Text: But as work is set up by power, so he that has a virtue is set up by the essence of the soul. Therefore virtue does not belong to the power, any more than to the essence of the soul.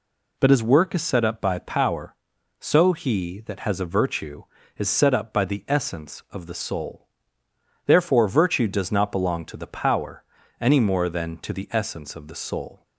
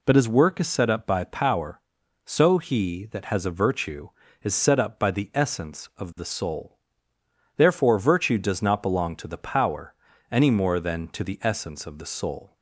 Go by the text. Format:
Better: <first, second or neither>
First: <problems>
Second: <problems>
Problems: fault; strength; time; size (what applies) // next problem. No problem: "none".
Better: neither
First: none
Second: none